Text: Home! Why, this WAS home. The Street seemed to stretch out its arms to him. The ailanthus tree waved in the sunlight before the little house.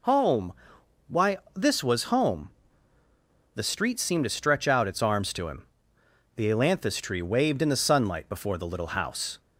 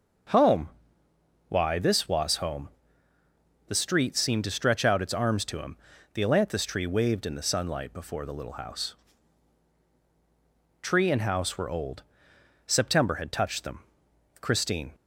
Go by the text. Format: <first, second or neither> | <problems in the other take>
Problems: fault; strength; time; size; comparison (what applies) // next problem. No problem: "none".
first | goes on to say "Tree and house were old September had touched them Christine"; strong; from 10.8 s on; 4.1 s long